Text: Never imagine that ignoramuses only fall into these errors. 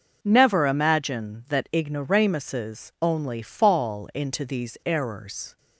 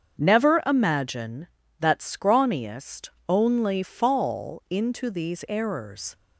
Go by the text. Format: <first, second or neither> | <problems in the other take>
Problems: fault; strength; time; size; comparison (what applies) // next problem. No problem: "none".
first | starts louder than the rest; strong; until 1.2 s; 7.5 dB // says "scrawniest" for "ignoramuses"; at 1.9 s